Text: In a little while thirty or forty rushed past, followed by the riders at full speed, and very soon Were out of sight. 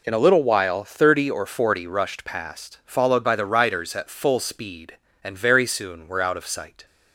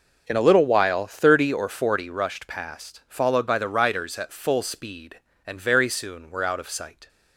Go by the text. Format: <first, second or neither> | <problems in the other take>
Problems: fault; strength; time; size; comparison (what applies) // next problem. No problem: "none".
first | starts louder than the rest; noticeable; until 1.9 s; 5.5 dB